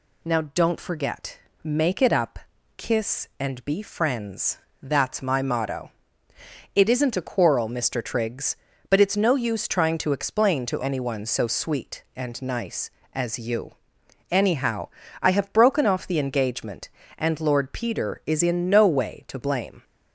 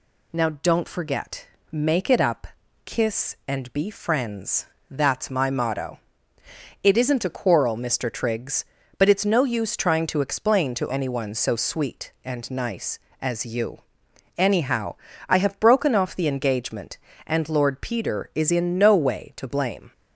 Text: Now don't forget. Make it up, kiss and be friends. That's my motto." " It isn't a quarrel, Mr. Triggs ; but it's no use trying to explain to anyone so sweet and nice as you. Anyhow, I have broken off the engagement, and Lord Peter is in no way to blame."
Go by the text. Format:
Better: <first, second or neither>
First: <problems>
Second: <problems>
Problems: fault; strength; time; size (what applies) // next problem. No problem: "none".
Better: neither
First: none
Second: none